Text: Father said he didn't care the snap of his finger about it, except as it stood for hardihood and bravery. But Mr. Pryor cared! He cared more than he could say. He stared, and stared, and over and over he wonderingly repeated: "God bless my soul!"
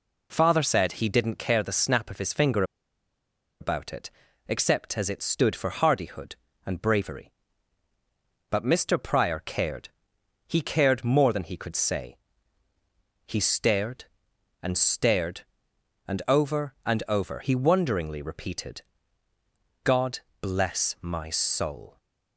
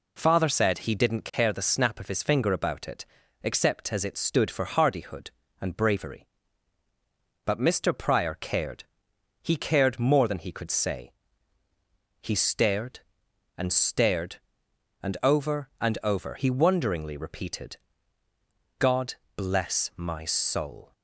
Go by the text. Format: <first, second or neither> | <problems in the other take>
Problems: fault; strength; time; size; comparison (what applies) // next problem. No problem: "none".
second | pauses between "finger" and "about"; noticeable; at 2.6 s; 0.97 s long // pauses between "God" and "bless"; slight; at 20.1 s; 0.22 s long; slight in the second